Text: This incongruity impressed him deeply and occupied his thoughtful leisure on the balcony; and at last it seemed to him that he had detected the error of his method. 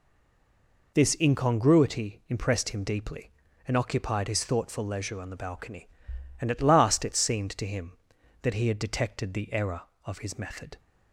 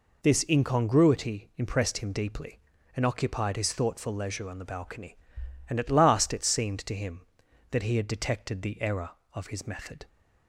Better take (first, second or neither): second